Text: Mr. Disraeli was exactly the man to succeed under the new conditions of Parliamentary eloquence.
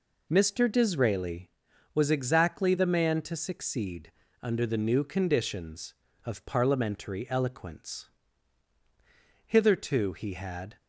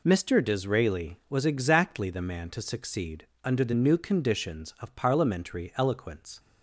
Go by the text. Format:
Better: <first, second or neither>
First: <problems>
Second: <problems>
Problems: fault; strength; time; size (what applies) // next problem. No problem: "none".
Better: second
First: pauses between "succeed" and "under"; slight; at 4.1 s; 0.28 s long // goes on to say "Hitherto he had"; noticeable; from 9.4 s on; 1.2 s long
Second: pauses between "succeed" and "under"; slight; at 3.2 s; 0.16 s long